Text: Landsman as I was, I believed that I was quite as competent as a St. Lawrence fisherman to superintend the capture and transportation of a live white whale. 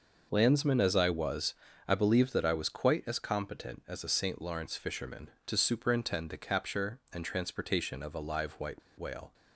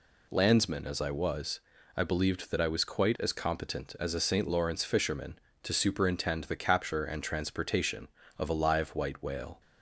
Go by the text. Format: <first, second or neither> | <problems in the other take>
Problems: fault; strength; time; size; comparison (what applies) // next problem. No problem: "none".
second | pauses between "white" and "whale"; slight; at 8.8 s; 0.18 s long